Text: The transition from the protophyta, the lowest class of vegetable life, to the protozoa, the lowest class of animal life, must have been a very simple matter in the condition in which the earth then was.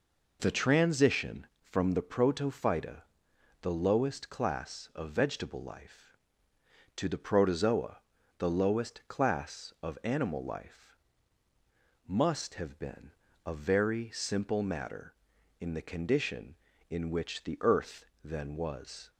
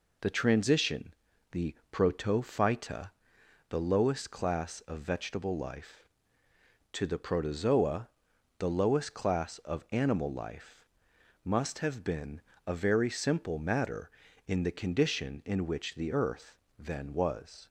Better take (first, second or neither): first